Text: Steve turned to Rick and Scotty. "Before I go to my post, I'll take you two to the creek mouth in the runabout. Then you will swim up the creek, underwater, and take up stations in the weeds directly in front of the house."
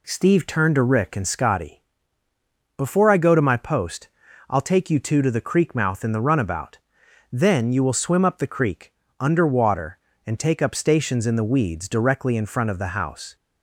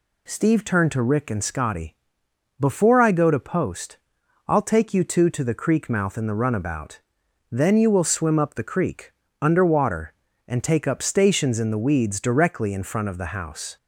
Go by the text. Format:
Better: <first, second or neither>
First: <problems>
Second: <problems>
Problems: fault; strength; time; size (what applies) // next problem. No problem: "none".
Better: first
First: none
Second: skips "my"; at 3.3 s